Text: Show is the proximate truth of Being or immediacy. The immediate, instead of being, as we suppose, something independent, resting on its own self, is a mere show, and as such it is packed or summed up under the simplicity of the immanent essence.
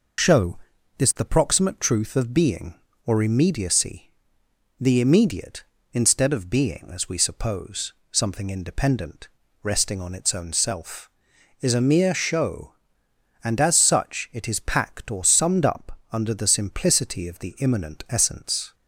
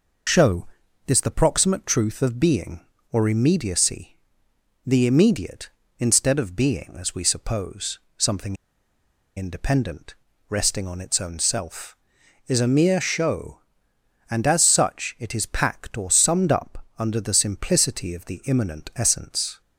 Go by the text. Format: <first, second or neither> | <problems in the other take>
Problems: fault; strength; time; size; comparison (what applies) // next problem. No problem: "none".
first | pauses between "something" and "independent"; noticeable; at 8.5 s; 0.82 s long